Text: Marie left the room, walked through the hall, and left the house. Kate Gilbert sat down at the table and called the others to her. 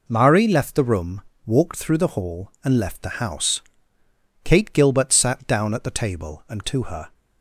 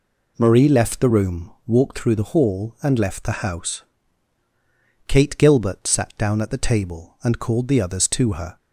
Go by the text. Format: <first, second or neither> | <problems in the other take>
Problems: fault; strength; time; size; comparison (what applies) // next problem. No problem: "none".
second | skips "called the others"; at 6.6 s